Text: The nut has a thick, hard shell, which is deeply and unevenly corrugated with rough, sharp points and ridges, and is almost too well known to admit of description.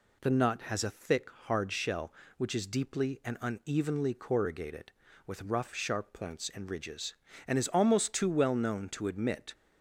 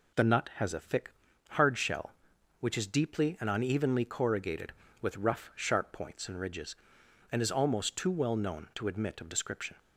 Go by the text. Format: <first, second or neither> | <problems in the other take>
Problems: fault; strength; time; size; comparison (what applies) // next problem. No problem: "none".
second | stops before "of description"; at 9.5 s